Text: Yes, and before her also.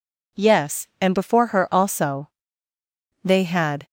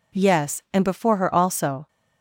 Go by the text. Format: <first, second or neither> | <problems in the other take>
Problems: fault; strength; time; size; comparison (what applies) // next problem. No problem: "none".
second | goes on to say "They had"; noticeable; from 3.2 s on; 0.62 s long